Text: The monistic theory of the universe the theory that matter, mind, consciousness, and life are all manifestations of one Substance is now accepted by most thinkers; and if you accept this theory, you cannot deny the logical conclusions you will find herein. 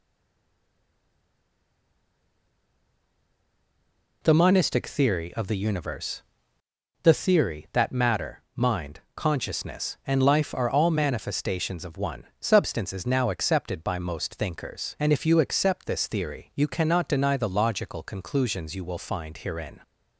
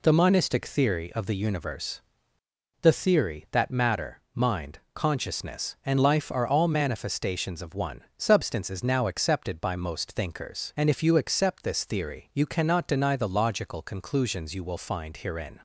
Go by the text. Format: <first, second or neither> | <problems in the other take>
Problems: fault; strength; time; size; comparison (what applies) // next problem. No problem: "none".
second | stays silent before the first word; strong; until 4.2 s; 4.2 s long // pauses between "universe" and "the"; noticeable; at 6.2 s; 0.82 s long; noticeable in the second // pauses between "one" and "Substance"; slight; at 12.2 s; 0.18 s long; slight in the second